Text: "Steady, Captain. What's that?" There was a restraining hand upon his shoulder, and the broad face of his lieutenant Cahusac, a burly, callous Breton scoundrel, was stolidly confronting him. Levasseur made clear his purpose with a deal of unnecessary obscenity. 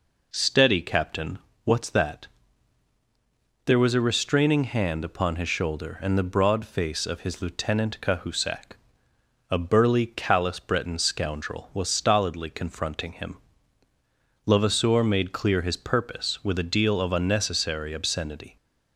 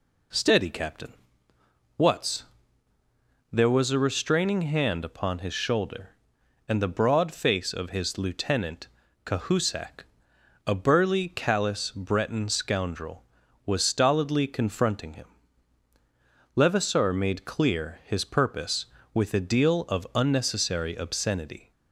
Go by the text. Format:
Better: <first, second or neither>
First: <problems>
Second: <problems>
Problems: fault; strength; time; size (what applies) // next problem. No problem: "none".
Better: first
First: none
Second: skips "that"; at 2.9 s // pauses between "lieutenant" and "Cahusac"; at 8.8 s; 0.38 s long